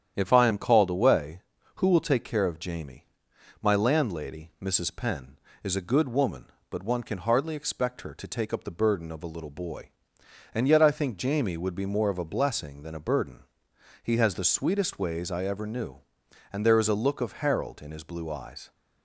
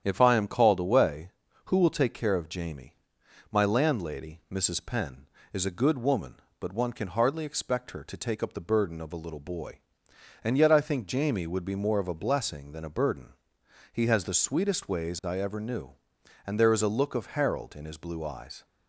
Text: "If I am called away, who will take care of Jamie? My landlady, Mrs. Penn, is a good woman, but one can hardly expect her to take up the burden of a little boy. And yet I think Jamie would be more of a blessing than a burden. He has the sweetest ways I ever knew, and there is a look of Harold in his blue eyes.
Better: neither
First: starts louder than the rest; strong; until 1.1 s; 9.5 dB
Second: starts louder than the rest; strong; until 1.0 s; 9.5 dB

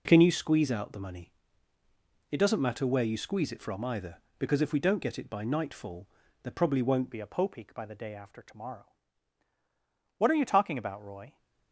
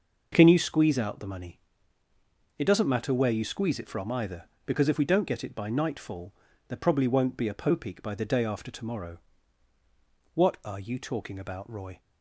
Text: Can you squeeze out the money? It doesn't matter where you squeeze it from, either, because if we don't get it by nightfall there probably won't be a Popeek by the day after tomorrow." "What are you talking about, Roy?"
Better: second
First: pauses between "nightfall" and "there"; at 6.0 s; 0.38 s long // changes voice at "be"; from 7.1 s on; 4.2 s long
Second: pauses between "nightfall" and "there"; at 6.3 s; 0.38 s long

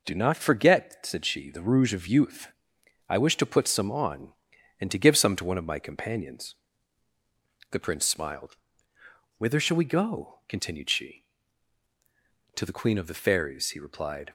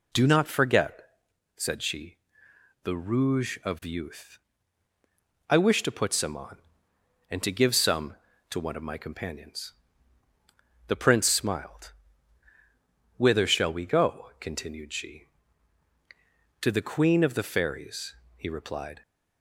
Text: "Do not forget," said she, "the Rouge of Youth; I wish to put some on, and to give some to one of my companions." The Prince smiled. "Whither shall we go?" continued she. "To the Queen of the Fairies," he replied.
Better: neither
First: none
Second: none

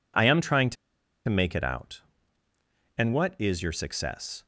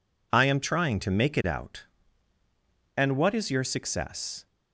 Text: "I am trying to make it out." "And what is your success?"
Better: second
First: pauses between "to" and "make"; noticeable; at 0.7 s; 0.53 s long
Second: none

